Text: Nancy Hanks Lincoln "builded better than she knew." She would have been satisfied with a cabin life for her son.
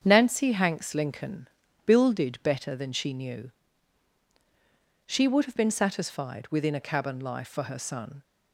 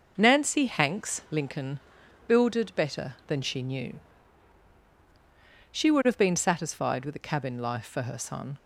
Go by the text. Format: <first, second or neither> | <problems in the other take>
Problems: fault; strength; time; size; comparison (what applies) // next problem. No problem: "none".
second | starts louder than the rest; strong; until 1.0 s; 7.5 dB // pauses between "Lincoln" and "builded"; at 1.4 s; 0.38 s long; noticeable in the second // says "within" for "with"; at 6.4 s